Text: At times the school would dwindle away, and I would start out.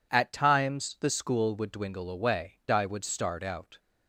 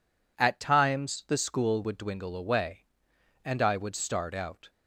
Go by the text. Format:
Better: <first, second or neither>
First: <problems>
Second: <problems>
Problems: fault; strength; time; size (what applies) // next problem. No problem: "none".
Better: second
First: skips "and"; at 2.6 s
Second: none